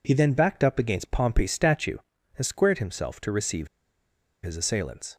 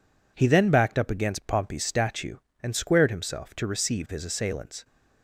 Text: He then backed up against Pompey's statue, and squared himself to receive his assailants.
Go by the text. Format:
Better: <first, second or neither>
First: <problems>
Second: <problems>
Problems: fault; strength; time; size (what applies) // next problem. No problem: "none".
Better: second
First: pauses between "receive" and "his"; noticeable; at 3.6 s; 0.77 s long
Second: none